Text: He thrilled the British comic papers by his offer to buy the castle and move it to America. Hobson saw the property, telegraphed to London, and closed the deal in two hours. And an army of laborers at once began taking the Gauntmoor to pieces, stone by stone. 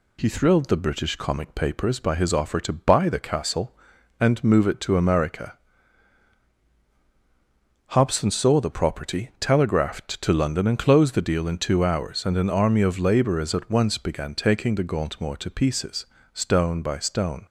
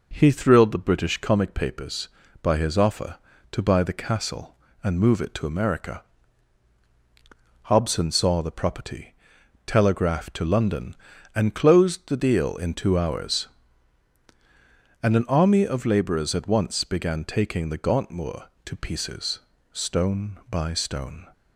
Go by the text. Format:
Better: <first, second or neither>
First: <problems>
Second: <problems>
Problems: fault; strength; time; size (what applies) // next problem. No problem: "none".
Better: neither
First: none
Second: none